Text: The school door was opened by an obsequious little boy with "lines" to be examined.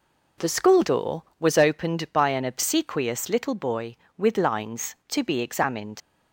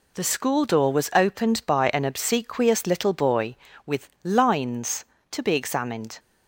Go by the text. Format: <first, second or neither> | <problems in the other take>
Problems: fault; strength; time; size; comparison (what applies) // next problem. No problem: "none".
second | leaves "examined" unfinished; at 6.0 s; 90 ms